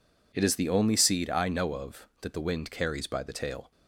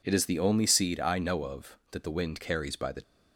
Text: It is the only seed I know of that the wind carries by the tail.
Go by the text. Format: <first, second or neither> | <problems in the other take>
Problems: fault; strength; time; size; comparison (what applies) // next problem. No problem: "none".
first | stops before "tail"; at 3.0 s